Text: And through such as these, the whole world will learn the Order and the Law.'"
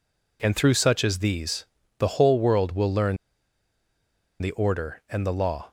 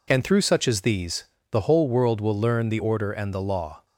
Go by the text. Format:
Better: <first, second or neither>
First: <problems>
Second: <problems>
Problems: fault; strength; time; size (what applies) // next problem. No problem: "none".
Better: second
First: pauses between "learn" and "the"; strong; at 3.1 s; 1.2 s long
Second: none